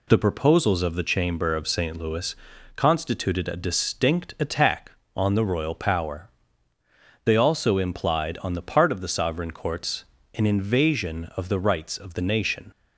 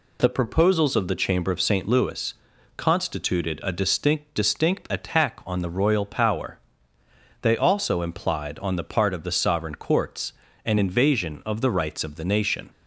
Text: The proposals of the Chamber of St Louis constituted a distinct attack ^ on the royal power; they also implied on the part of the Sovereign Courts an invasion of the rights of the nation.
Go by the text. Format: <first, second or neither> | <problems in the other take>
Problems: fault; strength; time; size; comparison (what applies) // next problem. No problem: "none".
first | pauses between "Louis" and "constituted"; at 2.3 s; 0.42 s long; also in the first // says "distinct" twice; at 4.3 s // pauses between "Courts" and "an"; slight; at 10.3 s; 0.32 s long; slight in the first